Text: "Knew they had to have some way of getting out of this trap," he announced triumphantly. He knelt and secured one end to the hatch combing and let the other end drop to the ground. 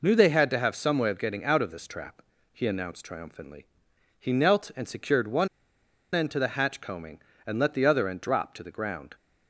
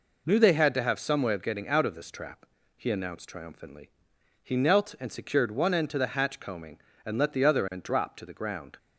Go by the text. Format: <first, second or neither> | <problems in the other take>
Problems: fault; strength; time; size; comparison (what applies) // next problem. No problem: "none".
second | pauses between "one" and "end"; noticeable; at 5.4 s; 0.67 s long